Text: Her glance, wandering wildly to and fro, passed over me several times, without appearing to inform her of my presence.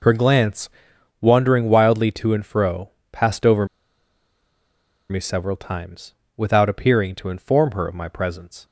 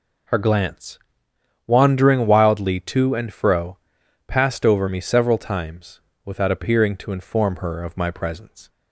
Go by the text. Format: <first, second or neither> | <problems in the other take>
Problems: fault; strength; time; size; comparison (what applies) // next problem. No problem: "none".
second | pauses between "over" and "me"; strong; at 3.6 s; 1.4 s long